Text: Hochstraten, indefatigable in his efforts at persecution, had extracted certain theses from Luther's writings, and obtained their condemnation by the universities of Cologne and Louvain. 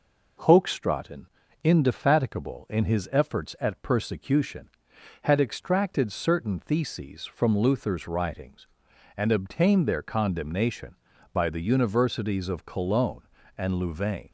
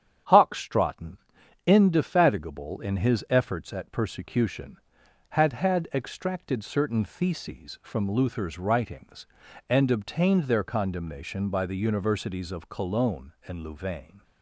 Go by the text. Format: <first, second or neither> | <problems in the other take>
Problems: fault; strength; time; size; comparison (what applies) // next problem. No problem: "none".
first | starts louder than the rest; strong; until 1.7 s; 9 dB // says "had" twice; at 5.5 s